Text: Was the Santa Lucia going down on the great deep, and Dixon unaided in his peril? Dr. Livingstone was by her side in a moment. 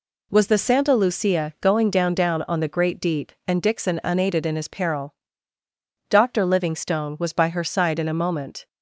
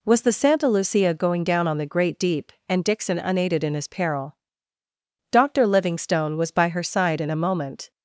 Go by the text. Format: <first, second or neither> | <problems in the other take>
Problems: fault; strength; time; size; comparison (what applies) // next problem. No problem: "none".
second | says "down" twice; at 2.1 s